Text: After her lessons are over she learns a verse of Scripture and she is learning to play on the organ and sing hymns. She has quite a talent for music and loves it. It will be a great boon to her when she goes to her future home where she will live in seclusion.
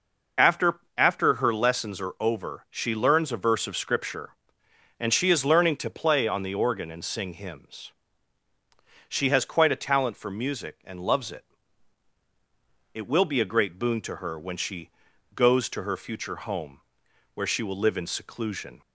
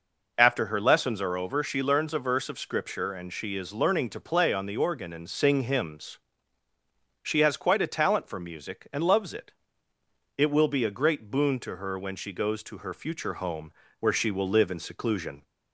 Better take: second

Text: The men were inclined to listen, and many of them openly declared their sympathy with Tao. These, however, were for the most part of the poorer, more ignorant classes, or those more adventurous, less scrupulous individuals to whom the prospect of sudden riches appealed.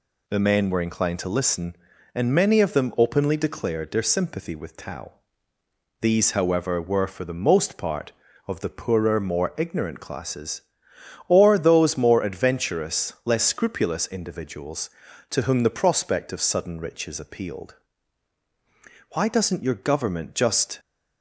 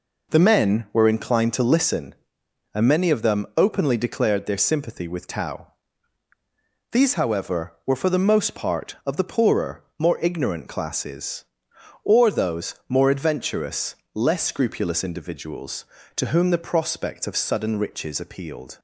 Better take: second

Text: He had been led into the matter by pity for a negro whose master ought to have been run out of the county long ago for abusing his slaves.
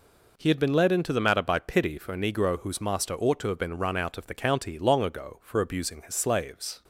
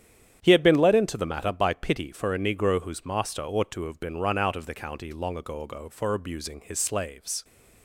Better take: first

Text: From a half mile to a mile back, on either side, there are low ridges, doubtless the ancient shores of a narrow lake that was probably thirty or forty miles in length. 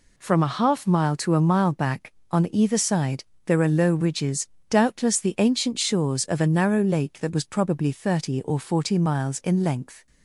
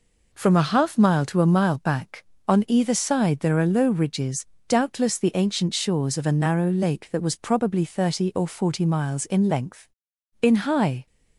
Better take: first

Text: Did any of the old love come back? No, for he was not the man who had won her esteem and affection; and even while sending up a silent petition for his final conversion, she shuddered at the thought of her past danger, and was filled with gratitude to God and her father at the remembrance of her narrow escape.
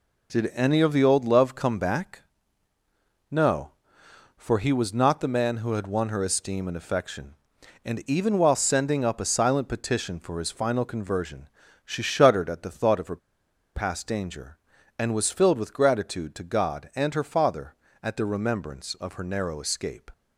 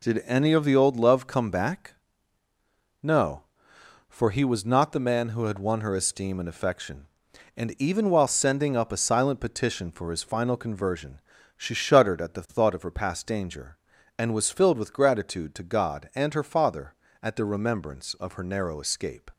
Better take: second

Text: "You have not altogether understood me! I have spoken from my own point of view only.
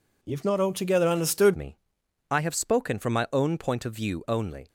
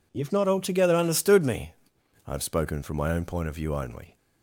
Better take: second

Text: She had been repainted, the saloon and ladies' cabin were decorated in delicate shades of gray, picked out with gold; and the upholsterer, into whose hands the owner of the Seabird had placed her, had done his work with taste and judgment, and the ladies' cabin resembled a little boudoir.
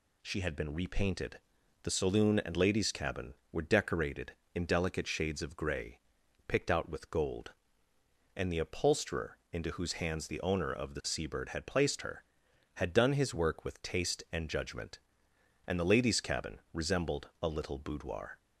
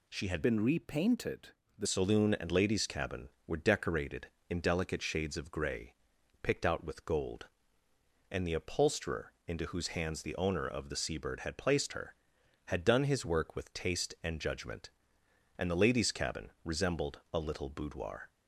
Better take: first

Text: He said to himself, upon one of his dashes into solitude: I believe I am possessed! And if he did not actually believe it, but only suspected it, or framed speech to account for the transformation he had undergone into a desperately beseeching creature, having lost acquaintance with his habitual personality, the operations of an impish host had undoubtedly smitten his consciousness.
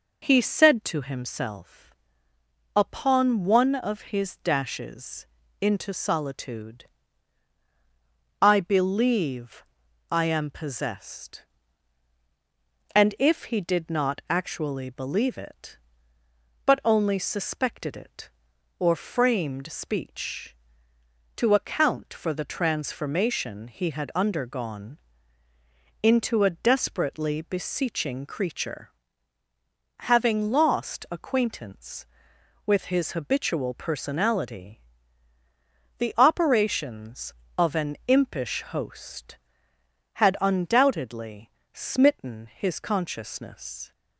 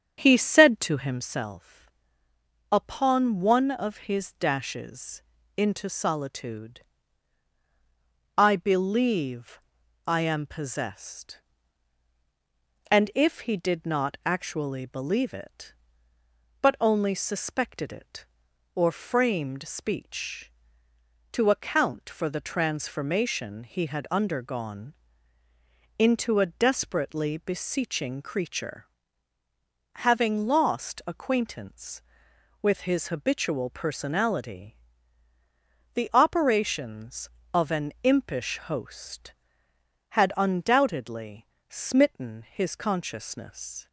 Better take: first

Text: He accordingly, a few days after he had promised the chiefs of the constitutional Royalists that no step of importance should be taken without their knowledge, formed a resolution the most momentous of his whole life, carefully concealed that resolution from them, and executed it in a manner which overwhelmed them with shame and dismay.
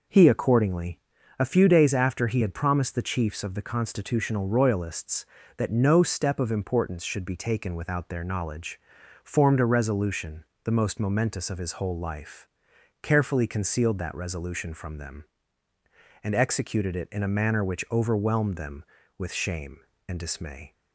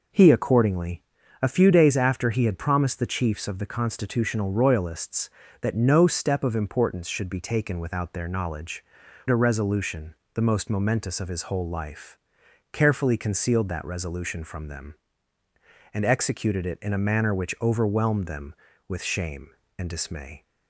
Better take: first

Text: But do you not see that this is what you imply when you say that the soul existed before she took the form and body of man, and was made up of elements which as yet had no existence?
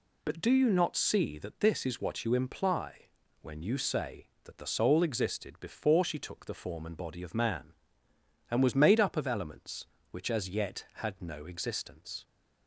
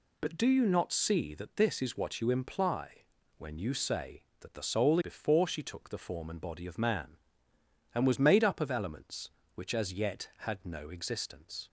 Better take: first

